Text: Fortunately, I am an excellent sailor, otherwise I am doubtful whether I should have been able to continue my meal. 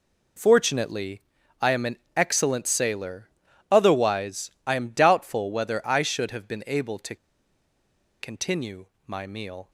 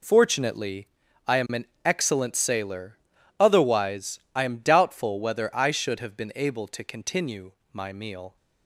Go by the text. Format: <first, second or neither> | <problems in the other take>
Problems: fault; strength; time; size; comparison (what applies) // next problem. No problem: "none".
second | pauses between "an" and "excellent"; slight; at 1.9 s; 0.18 s long; slight in the second // pauses between "otherwise" and "I"; slight; at 4.5 s; 0.16 s long; slight in the second // pauses between "to" and "continue"; at 7.1 s; 1.0 s long // pauses between "continue" and "my"; slight; at 8.8 s; 0.18 s long; slight in the second